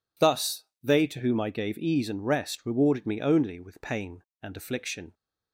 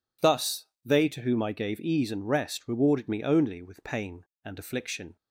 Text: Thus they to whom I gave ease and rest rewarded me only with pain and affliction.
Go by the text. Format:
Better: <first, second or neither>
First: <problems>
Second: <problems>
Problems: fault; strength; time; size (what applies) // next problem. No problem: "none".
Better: neither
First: pauses between "Thus" and "they"; slight; at 0.6 s; 0.18 s long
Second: pauses between "Thus" and "they"; slight; at 0.6 s; 0.18 s long